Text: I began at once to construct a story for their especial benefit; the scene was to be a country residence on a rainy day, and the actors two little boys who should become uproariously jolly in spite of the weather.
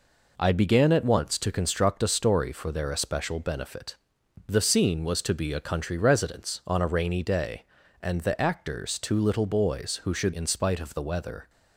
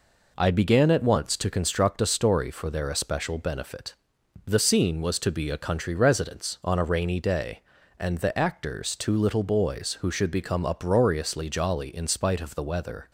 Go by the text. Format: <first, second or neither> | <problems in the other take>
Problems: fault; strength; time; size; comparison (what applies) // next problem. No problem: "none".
second | skips "become uproariously jolly"; at 10.3 s